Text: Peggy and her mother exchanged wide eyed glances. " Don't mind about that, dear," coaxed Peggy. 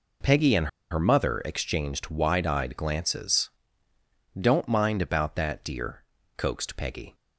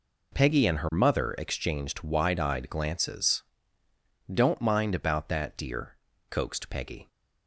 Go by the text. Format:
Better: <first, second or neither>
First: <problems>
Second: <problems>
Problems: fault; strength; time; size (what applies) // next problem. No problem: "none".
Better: second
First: pauses between "and" and "her"; slight; at 0.6 s; 0.23 s long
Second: none